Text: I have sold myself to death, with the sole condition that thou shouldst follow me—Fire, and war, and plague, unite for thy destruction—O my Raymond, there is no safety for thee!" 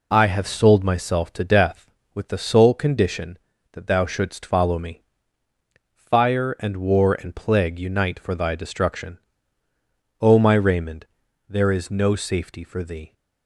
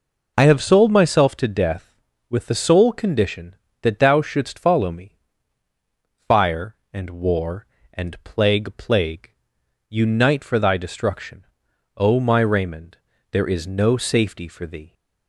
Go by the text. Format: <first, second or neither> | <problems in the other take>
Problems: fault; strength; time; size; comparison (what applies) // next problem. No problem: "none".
first | says "plague" twice; at 8.7 s